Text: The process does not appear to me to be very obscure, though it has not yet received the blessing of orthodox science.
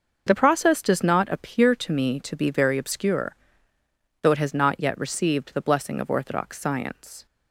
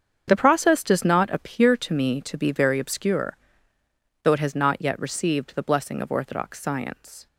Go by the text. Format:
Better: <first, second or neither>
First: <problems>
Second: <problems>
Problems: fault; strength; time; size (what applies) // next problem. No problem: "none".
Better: first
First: starts louder than the rest; noticeable; until 1.2 s; 6 dB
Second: gets quieter; strong; throughout; 13 dB // starts louder than the rest; strong; until 1.2 s; 7.5 dB